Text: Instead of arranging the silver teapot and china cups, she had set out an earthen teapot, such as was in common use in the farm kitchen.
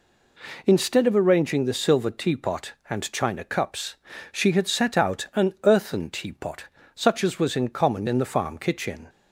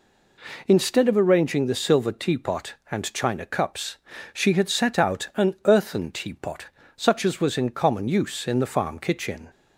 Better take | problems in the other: second | skips "use"; at 8.0 s

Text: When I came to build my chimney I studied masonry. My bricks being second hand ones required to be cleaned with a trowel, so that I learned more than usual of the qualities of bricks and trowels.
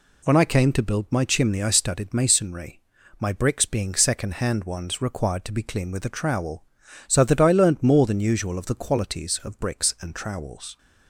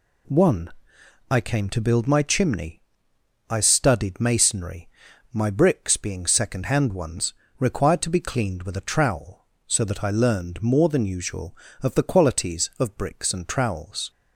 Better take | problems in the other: first | says "One" for "When"; at 0.2 s // pauses between "chimney" and "I"; noticeable; at 2.8 s; 0.66 s long // pauses between "ones" and "required"; slight; at 7.3 s; 0.28 s long

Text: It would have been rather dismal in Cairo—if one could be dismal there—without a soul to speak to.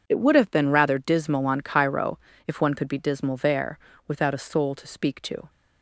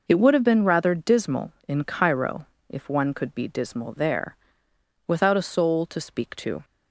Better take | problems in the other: second | says "on" for "in"; at 1.4 s

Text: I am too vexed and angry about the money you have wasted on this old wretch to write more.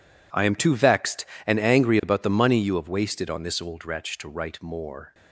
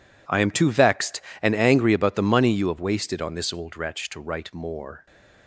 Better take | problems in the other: neither | none

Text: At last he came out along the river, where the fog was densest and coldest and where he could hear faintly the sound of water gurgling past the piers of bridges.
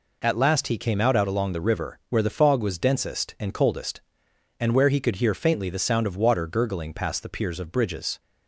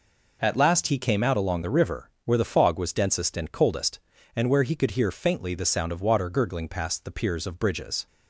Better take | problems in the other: second | says "out" twice; at 1.1 s

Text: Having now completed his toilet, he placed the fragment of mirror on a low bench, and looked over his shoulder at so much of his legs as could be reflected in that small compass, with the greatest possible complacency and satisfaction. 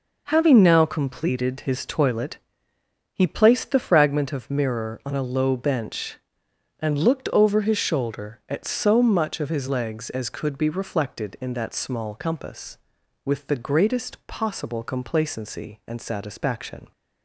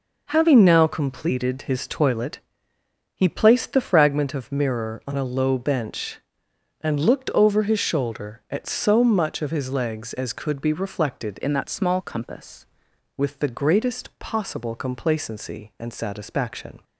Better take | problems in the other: first | changes voice from "in" to "compass"; from 11.4 to 12.6 s; 1.2 s long

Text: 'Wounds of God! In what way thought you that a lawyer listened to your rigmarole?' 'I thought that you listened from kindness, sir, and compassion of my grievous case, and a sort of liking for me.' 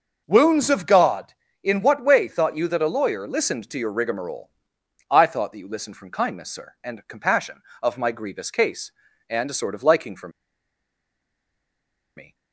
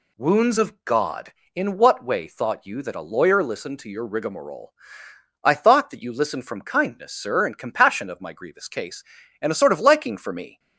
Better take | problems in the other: second | starts louder than the rest; until 1.2 s; 6.5 dB // pauses between "for" and "me"; strong; at 10.2 s; 1.8 s long

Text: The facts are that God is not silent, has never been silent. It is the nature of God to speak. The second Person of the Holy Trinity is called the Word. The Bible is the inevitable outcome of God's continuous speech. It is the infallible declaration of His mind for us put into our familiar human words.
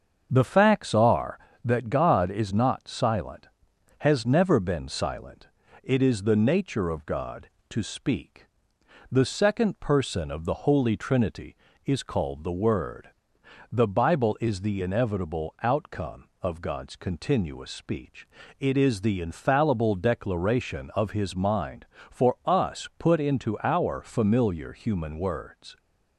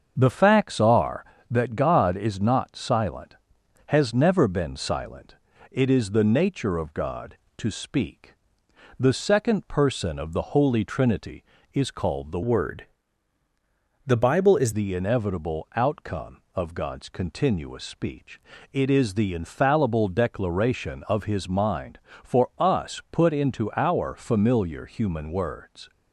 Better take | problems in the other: first | starts louder than the rest; until 1.1 s; 7 dB; also in the first // changes voice from "Word" to "is"; from 12.4 to 14.7 s; 2.3 s long

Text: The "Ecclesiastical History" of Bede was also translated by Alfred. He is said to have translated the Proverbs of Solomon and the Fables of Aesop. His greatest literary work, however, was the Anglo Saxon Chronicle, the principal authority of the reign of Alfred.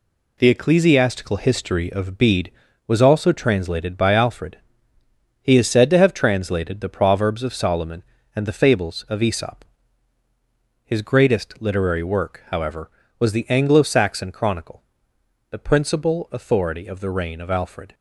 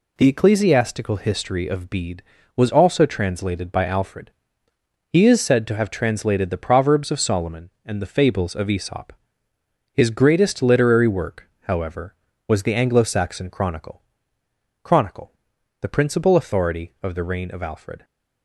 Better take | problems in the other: first | says "Chronicle" twice; at 14.8 s

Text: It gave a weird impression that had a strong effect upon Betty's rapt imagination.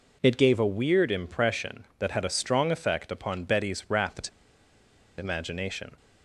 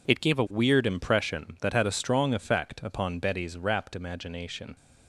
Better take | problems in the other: second | pauses between "rapt" and "imagination"; noticeable; at 4.2 s; 0.90 s long

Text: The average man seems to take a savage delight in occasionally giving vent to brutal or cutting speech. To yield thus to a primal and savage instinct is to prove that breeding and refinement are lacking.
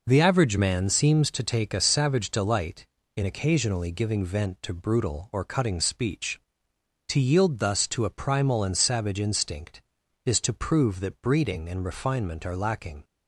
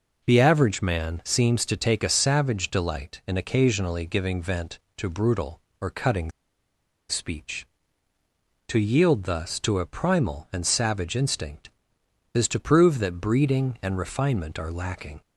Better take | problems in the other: first | pauses between "cutting" and "speech"; noticeable; at 6.3 s; 0.78 s long

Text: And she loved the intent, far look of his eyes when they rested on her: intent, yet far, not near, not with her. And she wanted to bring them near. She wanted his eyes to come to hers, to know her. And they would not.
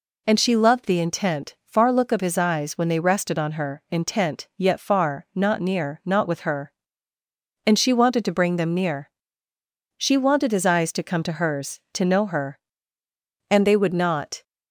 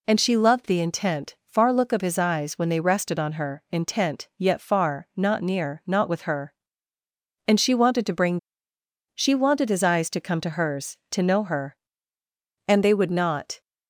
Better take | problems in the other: first | skips "them near"; at 8.7 s

